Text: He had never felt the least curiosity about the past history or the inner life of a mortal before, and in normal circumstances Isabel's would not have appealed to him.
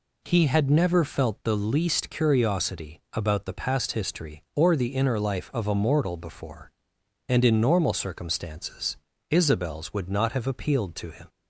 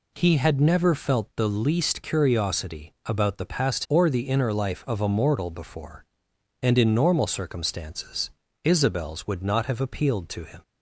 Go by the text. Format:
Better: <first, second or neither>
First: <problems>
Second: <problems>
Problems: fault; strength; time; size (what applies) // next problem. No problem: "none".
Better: first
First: pauses between "circumstances" and "Isabel's"; slight; at 8.9 s; 0.34 s long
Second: skips "history"; at 3.8 s // pauses between "circumstances" and "Isabel's"; slight; at 8.3 s; 0.34 s long